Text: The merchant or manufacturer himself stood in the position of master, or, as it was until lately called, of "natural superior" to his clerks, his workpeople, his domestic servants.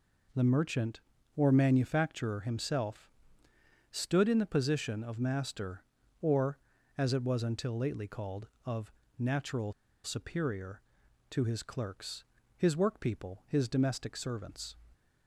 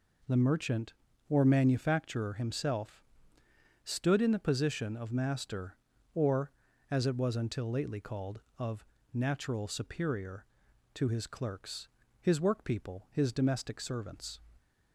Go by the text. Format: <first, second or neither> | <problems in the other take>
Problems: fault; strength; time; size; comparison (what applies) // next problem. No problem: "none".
second | pauses between "himself" and "stood"; noticeable; at 3.0 s; 0.80 s long; noticeable in the second // pauses between "of" and "natural"; slight; at 8.9 s; 0.26 s long; slight in the second // pauses between "natural" and "superior"; slight; at 9.7 s; 0.32 s long